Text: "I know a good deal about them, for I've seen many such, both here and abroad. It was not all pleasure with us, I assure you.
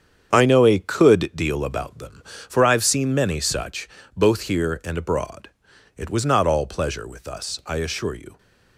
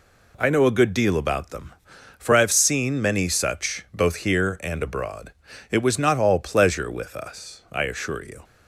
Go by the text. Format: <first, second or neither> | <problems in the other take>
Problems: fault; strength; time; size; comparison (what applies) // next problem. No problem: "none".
second | starts louder than the rest; strong; until 1.3 s; 8 dB // says "could" for "good"; at 0.7 s